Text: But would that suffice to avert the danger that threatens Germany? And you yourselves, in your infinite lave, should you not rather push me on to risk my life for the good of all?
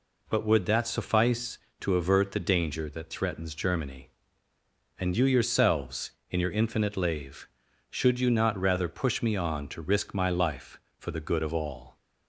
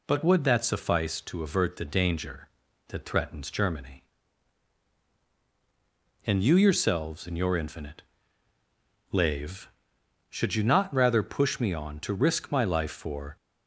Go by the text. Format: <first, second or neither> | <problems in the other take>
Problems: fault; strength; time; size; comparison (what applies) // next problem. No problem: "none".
first | pauses between "infinite" and "lave"; at 8.0 s; 1.1 s long // stops before "the good of all"; at 13.3 s